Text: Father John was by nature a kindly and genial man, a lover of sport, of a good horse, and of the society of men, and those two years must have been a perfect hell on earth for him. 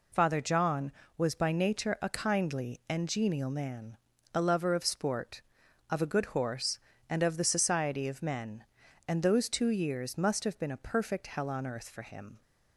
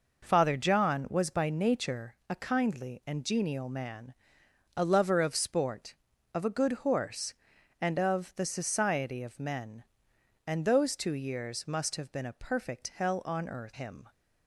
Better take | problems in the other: first | skips "for"; at 13.7 s

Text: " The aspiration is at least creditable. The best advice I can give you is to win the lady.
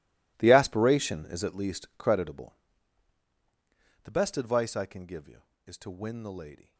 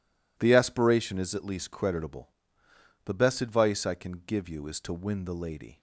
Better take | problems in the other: second | gets quieter; strong; throughout; 17 dB

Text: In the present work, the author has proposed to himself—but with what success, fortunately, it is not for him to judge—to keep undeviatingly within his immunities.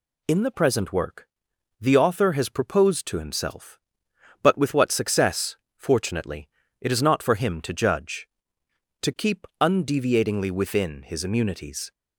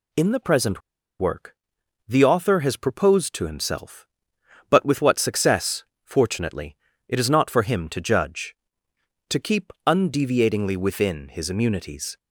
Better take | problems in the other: first | pauses between "present" and "work"; at 0.8 s; 0.39 s long

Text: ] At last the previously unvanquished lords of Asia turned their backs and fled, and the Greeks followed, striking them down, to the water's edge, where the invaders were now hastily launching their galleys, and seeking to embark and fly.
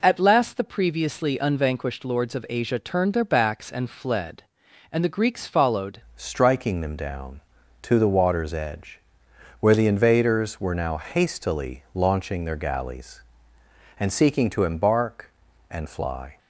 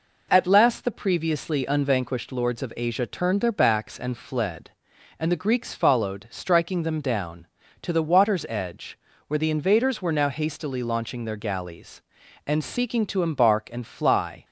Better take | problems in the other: second | changes voice at "striking"; from 6.1 s on; 10.2 s long

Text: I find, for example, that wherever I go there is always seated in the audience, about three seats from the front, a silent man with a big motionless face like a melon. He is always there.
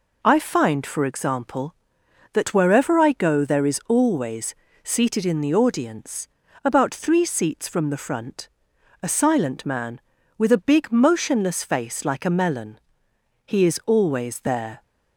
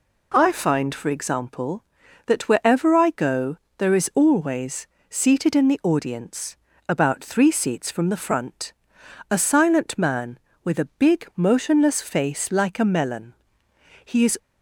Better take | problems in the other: first | pauses between "go" and "there"; slight; at 3.5 s; 0.20 s long // pauses between "always" and "seated"; slight; at 4.8 s; 0.24 s long; slight in the first // stops before "always there"; at 14.3 s

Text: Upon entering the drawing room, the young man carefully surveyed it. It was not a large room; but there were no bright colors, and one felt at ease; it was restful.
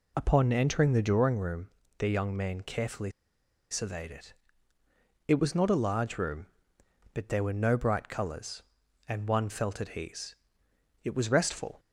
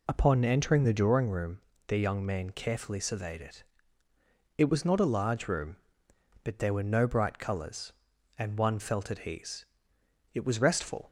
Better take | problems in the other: second | pauses between "carefully" and "surveyed"; noticeable; at 3.1 s; 0.60 s long

